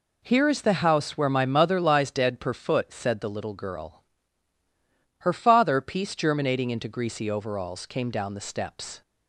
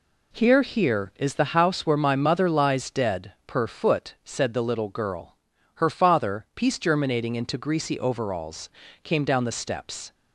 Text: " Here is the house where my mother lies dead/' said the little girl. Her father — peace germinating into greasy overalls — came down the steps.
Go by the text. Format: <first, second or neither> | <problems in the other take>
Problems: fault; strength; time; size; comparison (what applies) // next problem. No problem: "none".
first | says "Here" twice; at 0.6 s